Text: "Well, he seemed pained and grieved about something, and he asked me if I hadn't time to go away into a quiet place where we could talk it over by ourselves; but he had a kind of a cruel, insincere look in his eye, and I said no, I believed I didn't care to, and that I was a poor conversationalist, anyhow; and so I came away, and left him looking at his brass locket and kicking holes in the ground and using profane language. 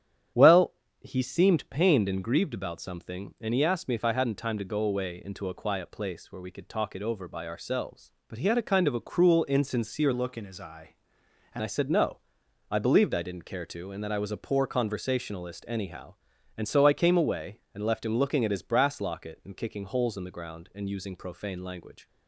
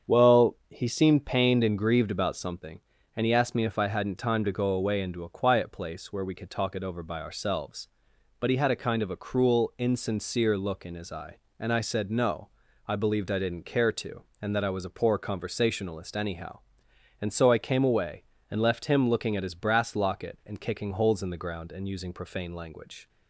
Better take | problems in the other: second | starts louder than the rest; strong; until 1.6 s; 9.5 dB; strong in the second // changes voice from "look" to "and"; from 10.1 to 11.6 s; 1.5 s long

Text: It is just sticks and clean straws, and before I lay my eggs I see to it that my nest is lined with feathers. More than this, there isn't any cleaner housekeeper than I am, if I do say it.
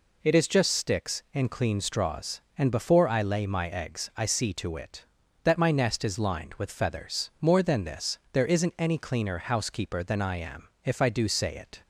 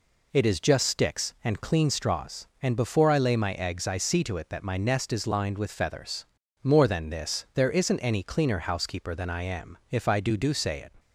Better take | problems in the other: first | says "do" twice; at 10.3 s

